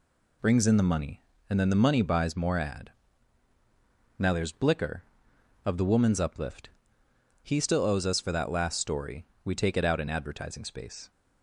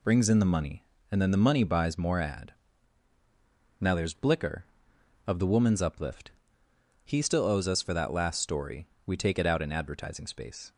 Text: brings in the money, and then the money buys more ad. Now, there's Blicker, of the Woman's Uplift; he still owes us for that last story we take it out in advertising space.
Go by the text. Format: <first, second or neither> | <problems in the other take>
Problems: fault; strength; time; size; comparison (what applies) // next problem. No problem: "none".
neither | pauses between "story" and "we"; slight; the same in both